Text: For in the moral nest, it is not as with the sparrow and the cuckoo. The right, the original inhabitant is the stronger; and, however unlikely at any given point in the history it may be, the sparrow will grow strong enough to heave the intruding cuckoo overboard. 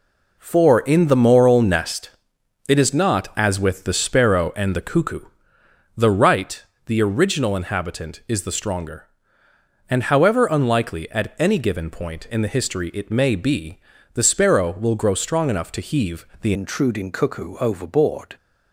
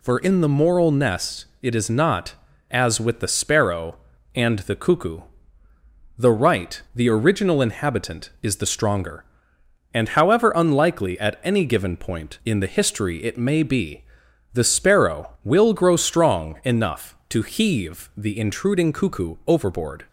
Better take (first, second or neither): second